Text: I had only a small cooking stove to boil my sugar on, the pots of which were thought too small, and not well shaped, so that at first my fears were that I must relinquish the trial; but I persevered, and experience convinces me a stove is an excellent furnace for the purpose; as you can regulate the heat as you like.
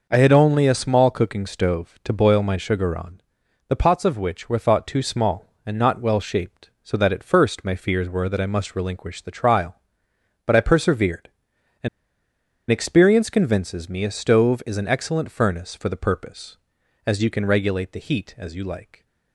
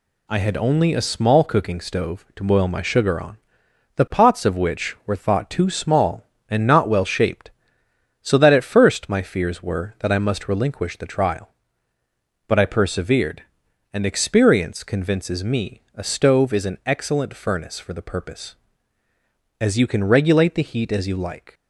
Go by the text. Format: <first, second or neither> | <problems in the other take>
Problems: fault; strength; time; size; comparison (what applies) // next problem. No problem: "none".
second | pauses between "and" and "experience"; noticeable; at 11.8 s; 0.80 s long